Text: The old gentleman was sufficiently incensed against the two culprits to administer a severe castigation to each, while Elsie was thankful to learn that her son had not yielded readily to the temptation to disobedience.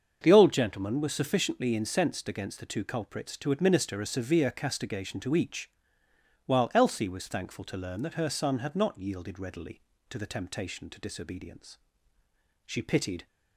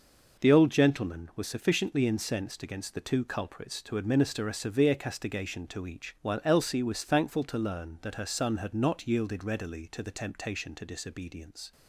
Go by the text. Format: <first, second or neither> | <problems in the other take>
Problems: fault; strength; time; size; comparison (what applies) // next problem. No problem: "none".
second | starts louder than the rest; until 1.2 s; 6.5 dB // goes on to say "She pitied"; from 12.6 s on; 0.60 s long